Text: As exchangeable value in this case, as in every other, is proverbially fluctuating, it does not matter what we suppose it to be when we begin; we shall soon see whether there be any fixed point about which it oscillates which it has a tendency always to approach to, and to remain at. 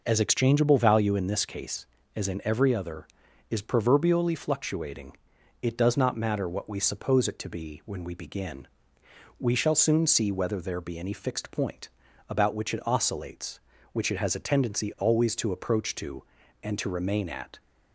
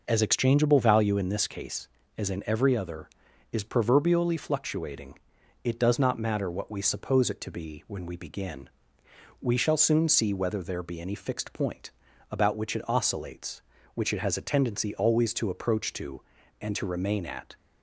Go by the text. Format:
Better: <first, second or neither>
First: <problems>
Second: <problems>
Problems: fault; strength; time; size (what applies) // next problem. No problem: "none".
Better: neither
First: pauses between "point" and "about"; at 11.8 s; 0.40 s long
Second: pauses between "point" and "about"; at 11.8 s; 0.40 s long